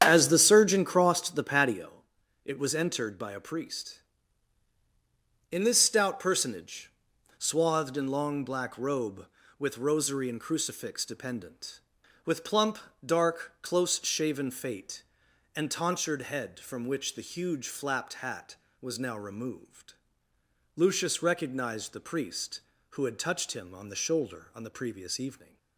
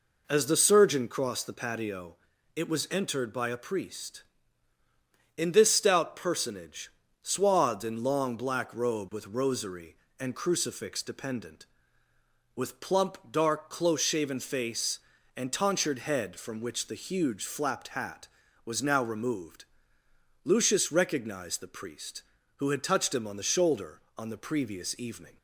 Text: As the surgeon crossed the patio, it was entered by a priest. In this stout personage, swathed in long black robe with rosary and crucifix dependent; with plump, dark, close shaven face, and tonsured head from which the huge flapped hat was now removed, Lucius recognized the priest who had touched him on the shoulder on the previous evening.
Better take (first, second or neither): second